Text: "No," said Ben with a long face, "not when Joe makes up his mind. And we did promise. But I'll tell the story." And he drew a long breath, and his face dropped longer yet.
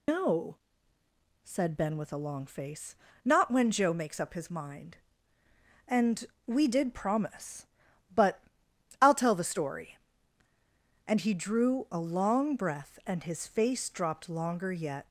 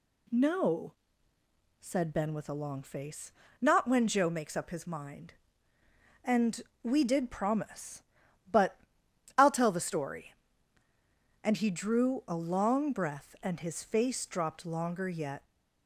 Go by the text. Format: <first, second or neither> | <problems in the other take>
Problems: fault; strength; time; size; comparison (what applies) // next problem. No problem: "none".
second | loses the start of "No"; at 0.0 s; 165 ms // pauses between "And" and "we"; slight; at 6.2 s; 0.22 s long; slight in the second // pauses between "But" and "I'll"; noticeable; at 8.4 s; 0.60 s long; noticeable in the second